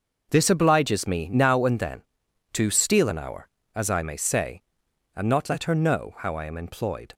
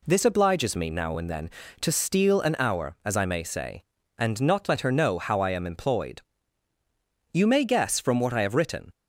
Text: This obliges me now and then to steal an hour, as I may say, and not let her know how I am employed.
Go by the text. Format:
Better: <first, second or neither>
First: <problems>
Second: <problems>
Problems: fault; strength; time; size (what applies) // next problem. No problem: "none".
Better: first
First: none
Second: goes on to say "You may guess from what I have written"; from 7.3 s on; 1.5 s long